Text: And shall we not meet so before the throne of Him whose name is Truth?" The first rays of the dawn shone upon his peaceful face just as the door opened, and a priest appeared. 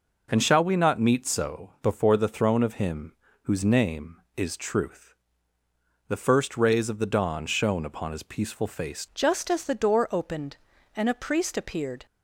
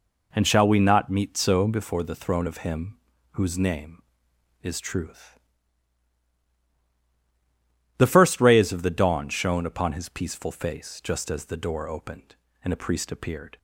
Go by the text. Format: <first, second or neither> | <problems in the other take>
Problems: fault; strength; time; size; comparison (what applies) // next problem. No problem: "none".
second | pauses between "Him" and "whose"; slight; at 3.1 s; 0.30 s long; slight in the second // changes voice at "just"; from 9.1 s on; 2.9 s long